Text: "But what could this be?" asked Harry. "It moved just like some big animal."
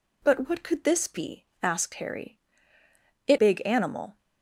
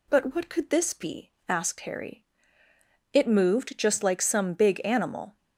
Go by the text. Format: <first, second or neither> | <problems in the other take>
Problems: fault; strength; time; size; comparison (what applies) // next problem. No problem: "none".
second | skips "moved just like some"; at 3.3 s